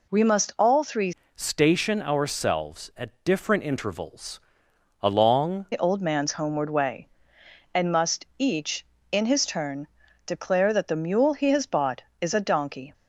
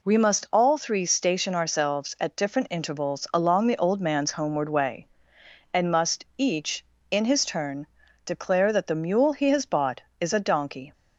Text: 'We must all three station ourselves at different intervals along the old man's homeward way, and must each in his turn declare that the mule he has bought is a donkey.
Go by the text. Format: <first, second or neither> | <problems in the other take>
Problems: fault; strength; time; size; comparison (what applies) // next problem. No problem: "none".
second | changes voice from "station" to "along"; from 1.3 to 5.6 s; 4.3 s long // pauses between "intervals" and "along"; noticeable; at 4.3 s; 0.62 s long // pauses between "turn" and "declare"; at 9.8 s; 0.40 s long; also in the second